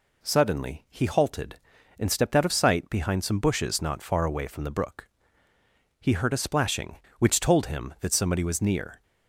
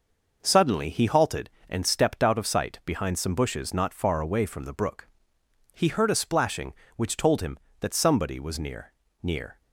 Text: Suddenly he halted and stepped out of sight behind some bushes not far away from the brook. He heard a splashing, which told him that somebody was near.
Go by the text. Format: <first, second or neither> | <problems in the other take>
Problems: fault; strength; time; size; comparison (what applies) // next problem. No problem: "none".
first | says "near" twice; at 9.2 s